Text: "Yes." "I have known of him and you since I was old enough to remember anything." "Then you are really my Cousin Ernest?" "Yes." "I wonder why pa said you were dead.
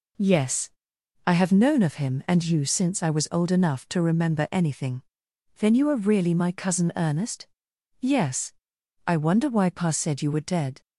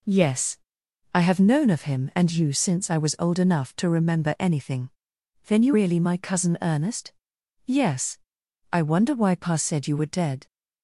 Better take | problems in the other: first | skips "are"; at 5.7 s

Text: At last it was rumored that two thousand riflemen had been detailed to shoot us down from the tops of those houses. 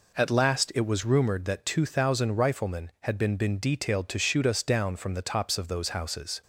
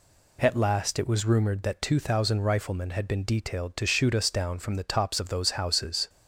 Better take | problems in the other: second | says "been" twice; at 3.3 s

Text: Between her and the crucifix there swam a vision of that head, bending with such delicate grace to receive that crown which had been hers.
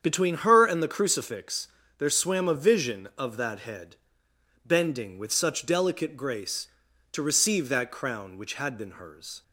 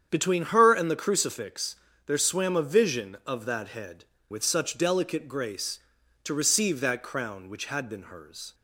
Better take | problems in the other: first | starts louder than the rest; strong; until 1.1 s; 8 dB; strong in the first // pauses between "crucifix" and "there"; slight; at 1.7 s; 0.32 s long; slight in the first // skips "bending"; at 4.1 s

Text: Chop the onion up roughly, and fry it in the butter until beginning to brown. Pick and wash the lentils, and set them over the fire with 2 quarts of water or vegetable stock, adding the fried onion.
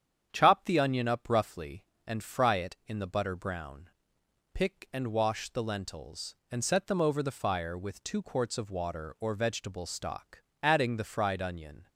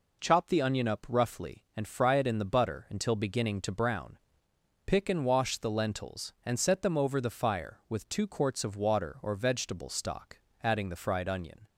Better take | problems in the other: second | starts louder than the rest; strong; until 1.3 s; 8.5 dB // skips "until beginning to"; at 3.3 s

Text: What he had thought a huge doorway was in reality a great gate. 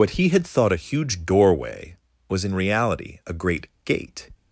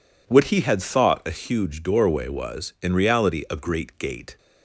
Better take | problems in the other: second | loses the start of "What"; at 0.0 s; 55 ms // pauses between "great" and "gate"; slight; at 3.6 s; 0.18 s long

